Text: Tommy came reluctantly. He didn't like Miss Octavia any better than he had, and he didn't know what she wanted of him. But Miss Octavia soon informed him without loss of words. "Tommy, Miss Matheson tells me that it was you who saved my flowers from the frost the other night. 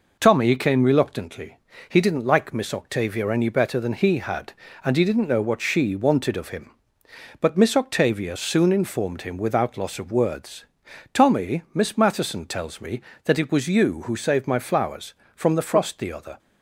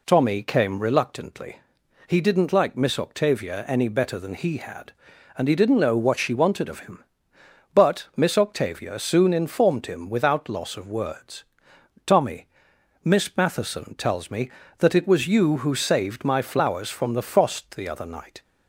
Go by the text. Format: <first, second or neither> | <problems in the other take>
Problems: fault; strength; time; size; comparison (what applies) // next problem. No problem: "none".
second | stops before "night"; at 16.3 s